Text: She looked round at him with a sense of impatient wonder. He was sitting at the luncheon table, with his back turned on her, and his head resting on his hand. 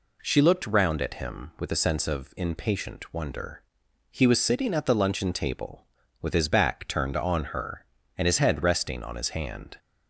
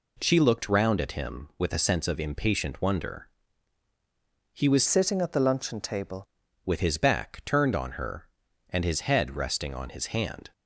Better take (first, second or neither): first